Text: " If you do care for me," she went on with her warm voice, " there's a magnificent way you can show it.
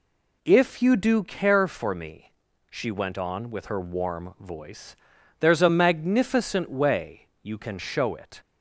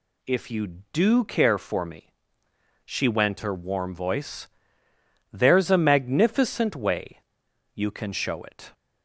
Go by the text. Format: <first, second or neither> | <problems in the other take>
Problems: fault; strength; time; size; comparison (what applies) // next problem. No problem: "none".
first | skips "on with"; at 3.4 s // pauses between "way" and "you"; noticeable; at 7.1 s; 0.54 s long; slight in the first